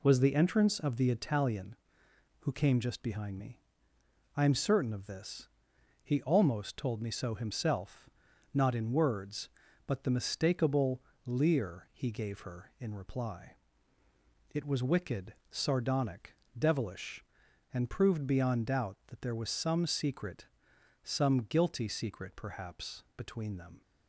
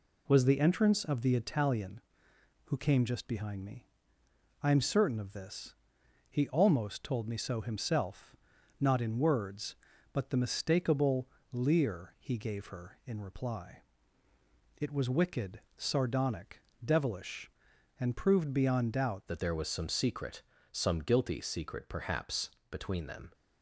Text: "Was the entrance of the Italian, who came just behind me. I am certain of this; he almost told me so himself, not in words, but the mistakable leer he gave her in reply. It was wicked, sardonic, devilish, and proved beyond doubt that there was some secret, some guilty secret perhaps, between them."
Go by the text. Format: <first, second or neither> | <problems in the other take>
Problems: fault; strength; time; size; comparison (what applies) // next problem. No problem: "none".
first | pauses between "mistakable" and "leer"; slight; at 11.2 s; 0.24 s long; slight in the first // changes voice at "that"; from 19.2 s on; 4.1 s long